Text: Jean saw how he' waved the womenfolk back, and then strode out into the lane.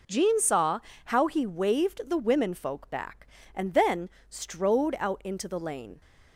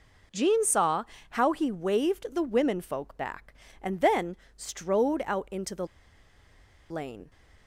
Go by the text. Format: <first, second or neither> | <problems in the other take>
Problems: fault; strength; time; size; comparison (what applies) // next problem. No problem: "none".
first | pauses between "saw" and "how"; slight; at 1.0 s; 0.26 s long; slight in the first // pauses between "then" and "strode"; slight; at 4.3 s; 0.20 s long; slight in the first // pauses between "the" and "lane"; at 5.8 s; 1.0 s long